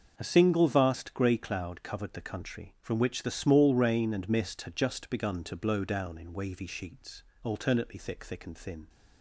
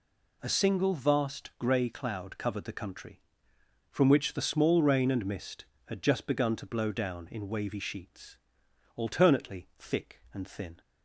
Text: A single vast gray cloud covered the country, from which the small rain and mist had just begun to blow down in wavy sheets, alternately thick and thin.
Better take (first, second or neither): second